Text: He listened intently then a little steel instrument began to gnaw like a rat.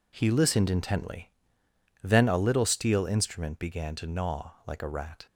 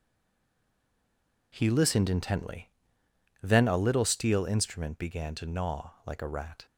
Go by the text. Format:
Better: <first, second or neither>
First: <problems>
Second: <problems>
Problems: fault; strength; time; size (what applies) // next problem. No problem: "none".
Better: first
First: pauses between "intently" and "then"; noticeable; at 1.3 s; 0.72 s long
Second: stays silent before the first word; noticeable; until 1.5 s; 1.5 s long // pauses between "intently" and "then"; noticeable; at 2.7 s; 0.72 s long